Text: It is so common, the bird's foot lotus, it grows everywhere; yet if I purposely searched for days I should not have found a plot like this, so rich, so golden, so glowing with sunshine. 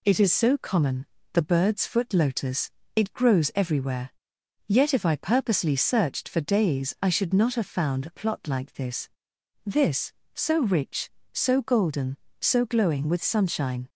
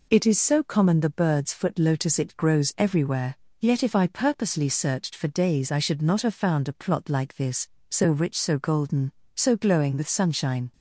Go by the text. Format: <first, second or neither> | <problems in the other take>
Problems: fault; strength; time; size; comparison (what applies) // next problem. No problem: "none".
second | says "this" twice; at 9.6 s